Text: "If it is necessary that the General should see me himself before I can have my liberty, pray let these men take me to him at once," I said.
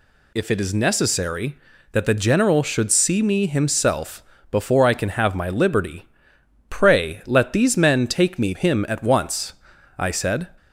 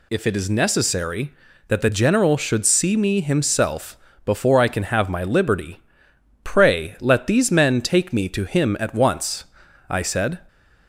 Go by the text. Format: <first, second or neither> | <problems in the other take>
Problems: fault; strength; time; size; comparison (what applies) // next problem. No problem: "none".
second | pauses between "himself" and "before"; slight; at 4.2 s; 0.28 s long; slight in the second // skips "to"; at 8.5 s